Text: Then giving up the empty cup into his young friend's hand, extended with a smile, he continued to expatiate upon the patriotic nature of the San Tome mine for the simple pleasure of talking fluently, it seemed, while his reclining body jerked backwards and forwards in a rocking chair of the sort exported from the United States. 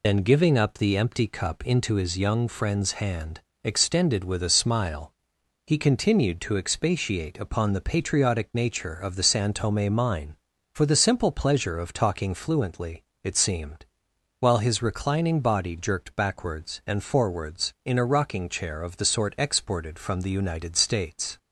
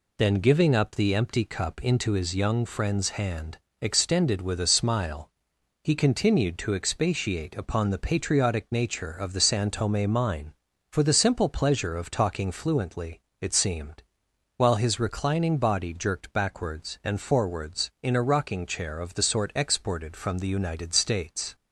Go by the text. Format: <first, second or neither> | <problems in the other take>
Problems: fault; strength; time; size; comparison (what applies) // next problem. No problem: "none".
second | loses the start of "Then"; at 0.0 s; 35 ms